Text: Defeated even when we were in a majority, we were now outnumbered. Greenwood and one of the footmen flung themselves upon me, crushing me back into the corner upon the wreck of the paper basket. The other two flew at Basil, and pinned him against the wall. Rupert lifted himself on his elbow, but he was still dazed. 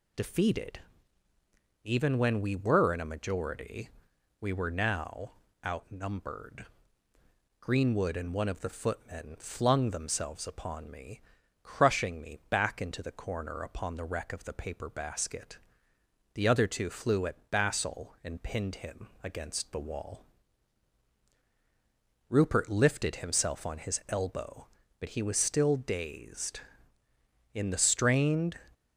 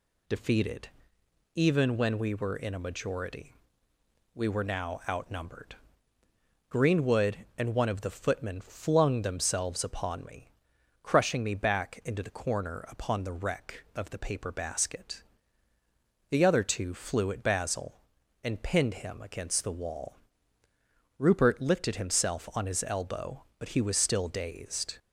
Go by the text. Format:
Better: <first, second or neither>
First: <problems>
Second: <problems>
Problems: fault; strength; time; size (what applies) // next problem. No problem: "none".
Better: second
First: pauses between "Defeated" and "even"; at 0.7 s; 1.0 s long // pauses between "now" and "outnumbered"; slight; at 5.3 s; 0.34 s long // goes on to say "In the strained"; noticeable; from 27.5 s on; 1.0 s long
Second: pauses between "Defeated" and "even"; noticeable; at 0.8 s; 0.66 s long